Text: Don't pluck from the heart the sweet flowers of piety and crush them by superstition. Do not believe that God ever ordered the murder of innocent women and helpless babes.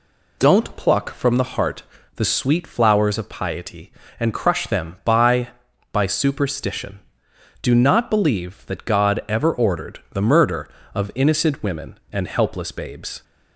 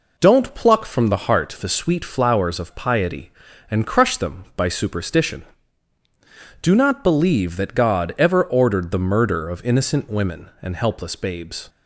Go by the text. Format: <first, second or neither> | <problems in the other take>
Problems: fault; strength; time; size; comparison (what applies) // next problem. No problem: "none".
second | pauses between "heart" and "the"; slight; at 1.8 s; 0.32 s long // says "by" twice; at 5.9 s